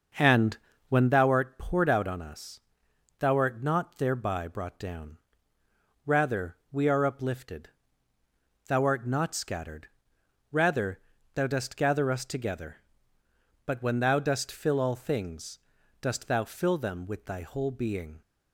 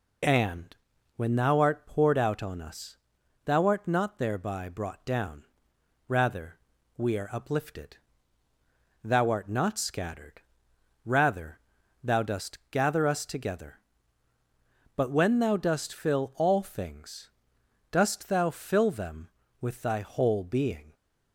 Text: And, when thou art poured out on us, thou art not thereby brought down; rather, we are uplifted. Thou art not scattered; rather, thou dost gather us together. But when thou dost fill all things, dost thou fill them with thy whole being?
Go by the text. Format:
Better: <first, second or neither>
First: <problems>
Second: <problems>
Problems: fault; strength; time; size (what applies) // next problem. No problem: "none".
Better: second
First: starts louder than the rest; noticeable; until 1.2 s; 6 dB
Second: none